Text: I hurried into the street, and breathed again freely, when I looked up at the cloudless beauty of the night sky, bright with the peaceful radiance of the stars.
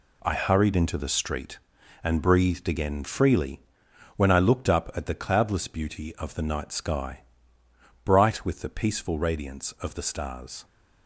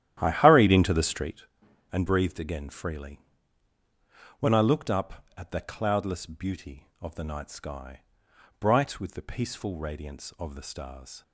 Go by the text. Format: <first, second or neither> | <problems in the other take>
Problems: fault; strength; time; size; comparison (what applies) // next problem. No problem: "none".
first | starts louder than the rest; strong; until 1.3 s; 11.5 dB